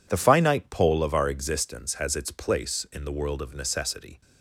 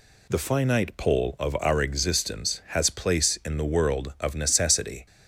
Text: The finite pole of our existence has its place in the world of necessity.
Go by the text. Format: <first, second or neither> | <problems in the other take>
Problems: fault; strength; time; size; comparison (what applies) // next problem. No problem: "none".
first | skips "its"; at 2.8 s